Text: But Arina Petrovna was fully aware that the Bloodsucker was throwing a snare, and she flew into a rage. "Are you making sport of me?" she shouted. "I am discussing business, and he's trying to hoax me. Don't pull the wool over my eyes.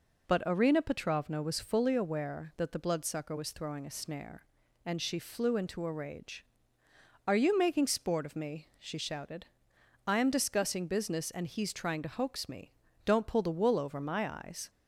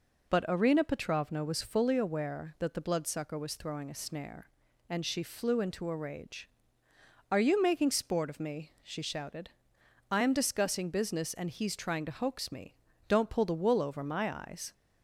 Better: neither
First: none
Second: none

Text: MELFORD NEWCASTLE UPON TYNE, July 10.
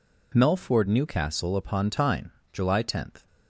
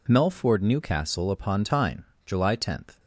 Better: neither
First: none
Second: none

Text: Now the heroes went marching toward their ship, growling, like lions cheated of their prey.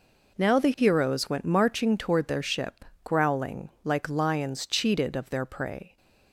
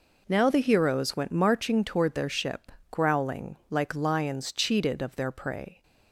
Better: neither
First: none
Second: none

